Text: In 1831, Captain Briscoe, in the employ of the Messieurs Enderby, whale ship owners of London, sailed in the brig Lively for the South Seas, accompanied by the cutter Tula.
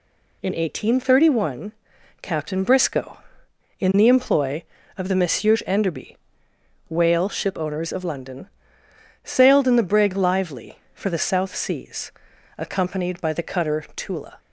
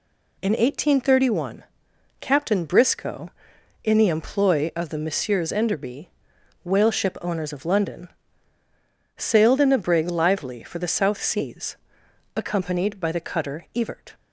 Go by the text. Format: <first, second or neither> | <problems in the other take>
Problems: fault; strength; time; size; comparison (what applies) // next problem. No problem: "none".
first | says "Evert" for "Tula"; at 13.7 s